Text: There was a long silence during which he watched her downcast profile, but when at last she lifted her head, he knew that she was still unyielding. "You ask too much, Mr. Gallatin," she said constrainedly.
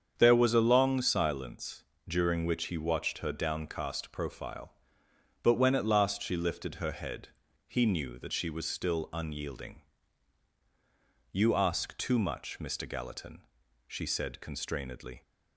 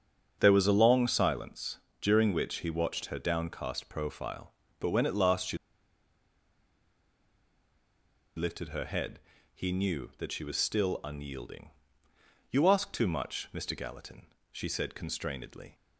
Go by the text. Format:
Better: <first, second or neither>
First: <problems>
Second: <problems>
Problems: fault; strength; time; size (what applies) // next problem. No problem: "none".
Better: first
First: starts louder than the rest; strong; until 1.1 s; 7.5 dB // pauses between "silence" and "during"; slight; at 1.8 s; 0.24 s long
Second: starts louder than the rest; until 1.4 s; 7 dB // pauses between "silence" and "during"; slight; at 1.7 s; 0.20 s long // pauses between "she" and "lifted"; strong; at 5.5 s; 2.7 s long